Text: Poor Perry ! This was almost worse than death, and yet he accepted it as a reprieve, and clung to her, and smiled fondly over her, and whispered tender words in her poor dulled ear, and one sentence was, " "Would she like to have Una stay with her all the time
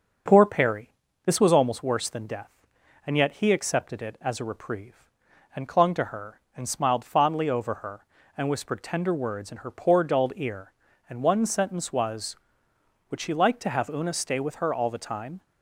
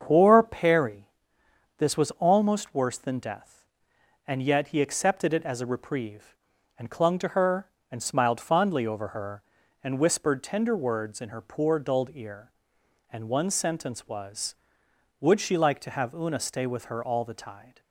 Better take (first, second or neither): first